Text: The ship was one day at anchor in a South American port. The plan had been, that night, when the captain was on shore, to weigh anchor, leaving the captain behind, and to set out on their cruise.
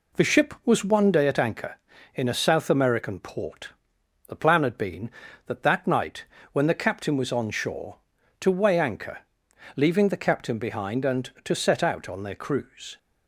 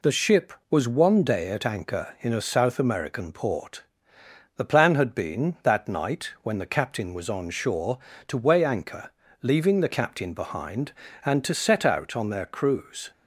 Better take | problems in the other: second | says "that" twice; at 5.6 s

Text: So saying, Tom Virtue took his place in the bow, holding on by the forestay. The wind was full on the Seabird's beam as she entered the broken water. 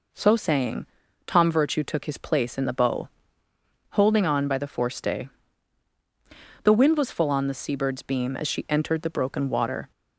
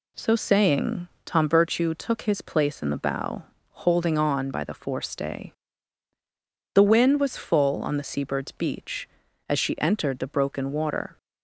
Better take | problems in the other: first | says "beach" for "beam"; at 8.5 s

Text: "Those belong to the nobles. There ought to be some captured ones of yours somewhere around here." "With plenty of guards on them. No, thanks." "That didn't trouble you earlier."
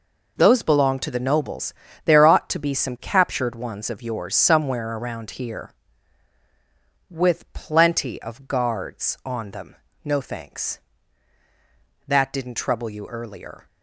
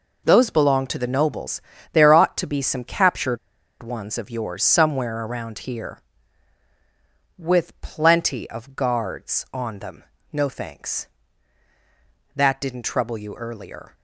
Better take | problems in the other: first | pauses between "captured" and "ones"; at 3.3 s; 0.44 s long

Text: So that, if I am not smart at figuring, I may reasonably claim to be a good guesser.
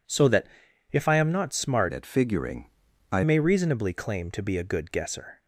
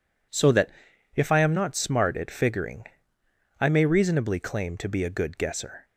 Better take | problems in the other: second | changes voice from "at" to "I"; from 1.9 to 3.2 s; 1.3 s long

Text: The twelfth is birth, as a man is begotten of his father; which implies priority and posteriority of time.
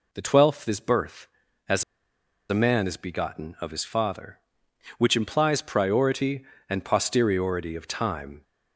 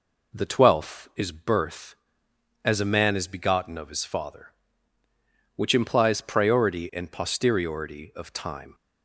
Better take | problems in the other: second | pauses between "as" and "a"; noticeable; at 1.8 s; 0.67 s long

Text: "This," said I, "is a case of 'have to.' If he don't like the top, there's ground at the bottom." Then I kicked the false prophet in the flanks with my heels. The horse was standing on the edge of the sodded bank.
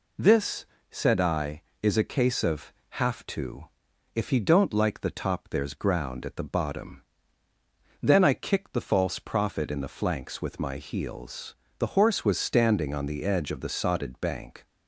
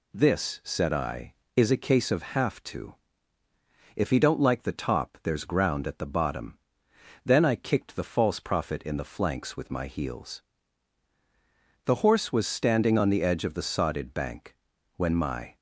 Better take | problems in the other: first | goes on to say "When my"; from 14.9 s on; 0.58 s long

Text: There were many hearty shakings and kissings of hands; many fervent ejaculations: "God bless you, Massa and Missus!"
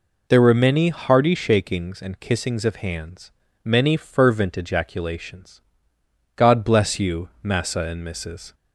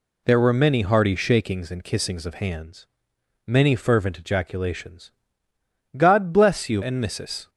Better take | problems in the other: first | skips "Massa"; at 6.8 s

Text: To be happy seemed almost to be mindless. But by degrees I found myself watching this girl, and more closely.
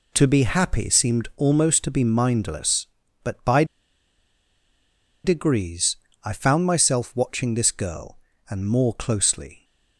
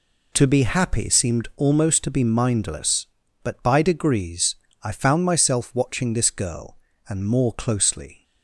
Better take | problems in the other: second | pauses between "by" and "degrees"; strong; at 3.6 s; 1.6 s long // pauses between "degrees" and "I"; slight; at 5.9 s; 0.28 s long; slight in the second

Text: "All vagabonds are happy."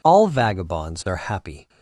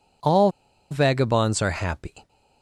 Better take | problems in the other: first | pauses between "All" and "vagabonds"; at 0.5 s; 0.40 s long

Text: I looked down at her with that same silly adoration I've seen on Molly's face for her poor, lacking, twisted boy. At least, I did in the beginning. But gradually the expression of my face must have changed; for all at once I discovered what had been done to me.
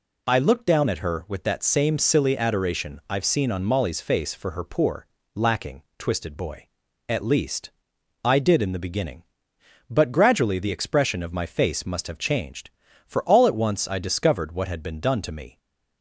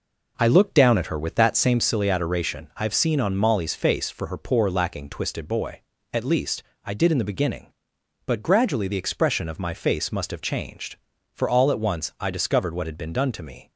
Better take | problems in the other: first | starts louder than the rest; noticeable; until 1.9 s; 4.5 dB

